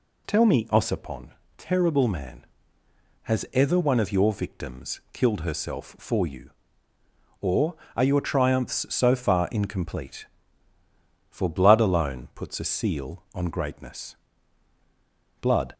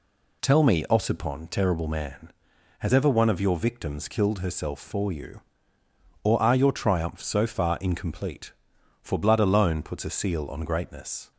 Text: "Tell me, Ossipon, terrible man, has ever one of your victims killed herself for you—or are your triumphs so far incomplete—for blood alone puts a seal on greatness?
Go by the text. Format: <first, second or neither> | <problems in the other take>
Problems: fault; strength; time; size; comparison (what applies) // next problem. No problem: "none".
second | goes on to say "Blood"; slight; from 15.3 s on; 0.34 s long